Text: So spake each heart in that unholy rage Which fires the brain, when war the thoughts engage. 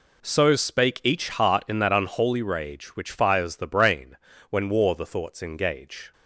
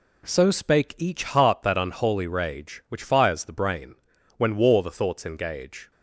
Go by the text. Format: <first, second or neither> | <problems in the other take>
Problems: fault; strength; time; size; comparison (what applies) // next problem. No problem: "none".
first | skips "in"; at 1.6 s